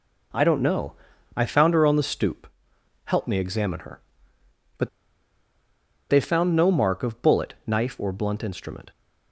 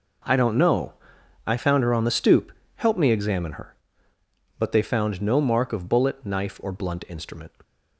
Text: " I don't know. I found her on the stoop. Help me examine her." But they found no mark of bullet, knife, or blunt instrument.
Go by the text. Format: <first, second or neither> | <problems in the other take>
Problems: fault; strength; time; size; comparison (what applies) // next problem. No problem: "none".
second | pauses between "But" and "they"; at 4.8 s; 1.2 s long